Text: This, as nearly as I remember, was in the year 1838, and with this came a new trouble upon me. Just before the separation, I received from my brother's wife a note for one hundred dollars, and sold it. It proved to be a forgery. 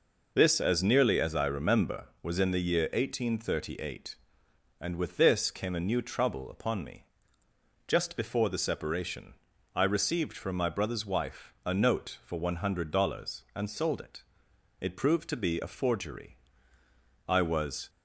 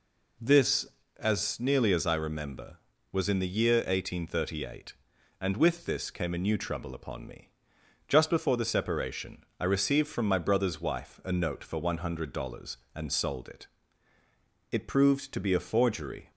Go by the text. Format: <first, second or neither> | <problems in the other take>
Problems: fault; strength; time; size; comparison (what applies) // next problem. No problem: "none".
second | goes on to say "I was"; noticeable; from 17.2 s on; 0.62 s long